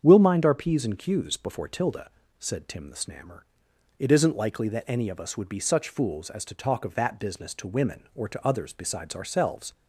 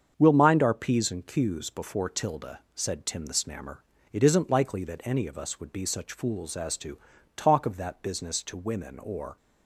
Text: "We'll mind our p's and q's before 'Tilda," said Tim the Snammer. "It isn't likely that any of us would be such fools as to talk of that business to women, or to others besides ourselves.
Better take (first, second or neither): first